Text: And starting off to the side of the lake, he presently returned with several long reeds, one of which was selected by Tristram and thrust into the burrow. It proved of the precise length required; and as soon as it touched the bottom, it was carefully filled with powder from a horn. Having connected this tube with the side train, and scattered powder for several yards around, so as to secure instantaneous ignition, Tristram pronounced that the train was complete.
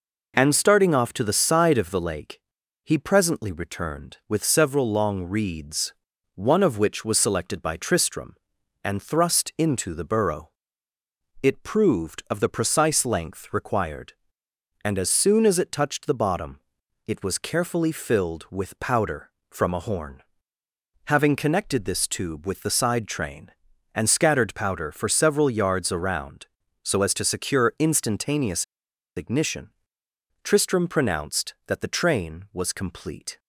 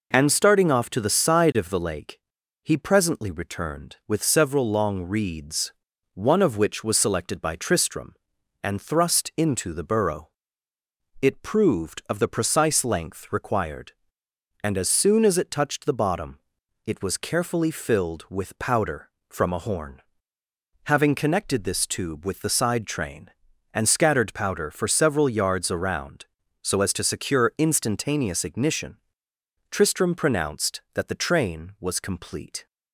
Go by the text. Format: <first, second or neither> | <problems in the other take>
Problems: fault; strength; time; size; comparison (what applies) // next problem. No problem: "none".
second | pauses between "instantaneous" and "ignition"; noticeable; at 28.6 s; 0.52 s long